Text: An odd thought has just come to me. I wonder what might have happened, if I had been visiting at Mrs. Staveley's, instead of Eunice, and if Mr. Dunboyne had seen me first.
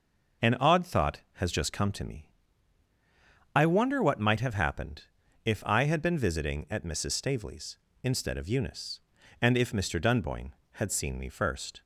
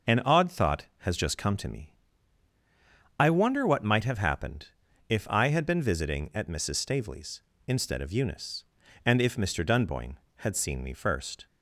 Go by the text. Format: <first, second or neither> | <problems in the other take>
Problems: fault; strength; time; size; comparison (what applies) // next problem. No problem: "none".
neither | none